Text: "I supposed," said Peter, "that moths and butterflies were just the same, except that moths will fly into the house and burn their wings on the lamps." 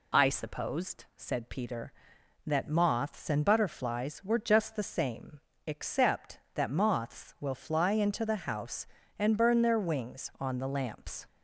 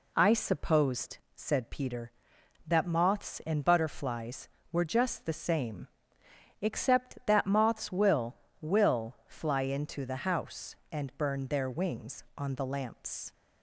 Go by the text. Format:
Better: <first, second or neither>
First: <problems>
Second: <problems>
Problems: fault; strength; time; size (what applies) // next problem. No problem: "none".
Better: first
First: none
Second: says "will" twice; at 8.6 s